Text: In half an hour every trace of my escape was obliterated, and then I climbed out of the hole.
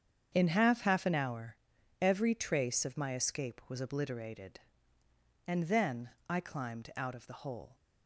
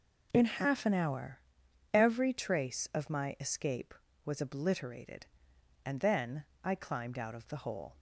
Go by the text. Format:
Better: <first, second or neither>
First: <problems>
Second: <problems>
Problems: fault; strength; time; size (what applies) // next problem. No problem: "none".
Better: second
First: starts louder than the rest; strong; until 1.3 s; 7.5 dB // says "half" twice; at 0.8 s // pauses between "hour" and "every"; at 1.5 s; 0.44 s long // pauses between "then" and "I"; slight; at 6.0 s; 0.18 s long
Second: pauses between "hour" and "every"; noticeable; at 1.4 s; 0.52 s long // pauses between "then" and "I"; slight; at 6.4 s; 0.18 s long